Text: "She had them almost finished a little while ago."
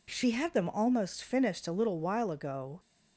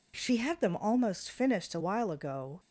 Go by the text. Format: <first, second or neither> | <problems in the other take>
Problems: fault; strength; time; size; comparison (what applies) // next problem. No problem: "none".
first | skips "little"; at 1.7 s